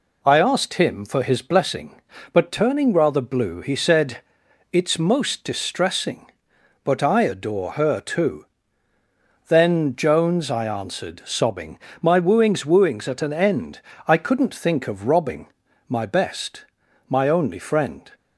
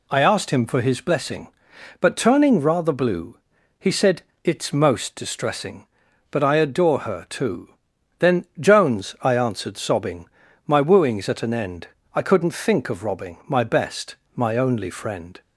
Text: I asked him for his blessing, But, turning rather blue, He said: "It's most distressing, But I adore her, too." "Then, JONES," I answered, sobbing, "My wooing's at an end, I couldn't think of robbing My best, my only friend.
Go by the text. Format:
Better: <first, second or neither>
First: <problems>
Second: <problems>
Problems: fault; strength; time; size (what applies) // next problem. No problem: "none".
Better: second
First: says "wooing's" twice; at 12.6 s // pauses between "robbing" and "My"; at 15.4 s; 0.40 s long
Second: none